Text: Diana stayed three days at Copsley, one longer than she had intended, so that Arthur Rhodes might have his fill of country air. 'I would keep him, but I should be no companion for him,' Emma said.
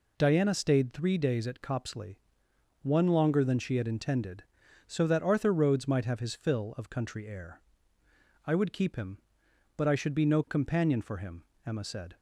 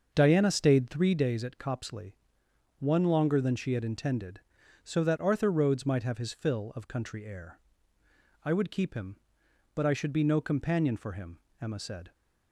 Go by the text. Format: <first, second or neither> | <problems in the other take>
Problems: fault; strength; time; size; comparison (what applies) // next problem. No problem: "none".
first | starts louder than the rest; until 1.3 s; 6.5 dB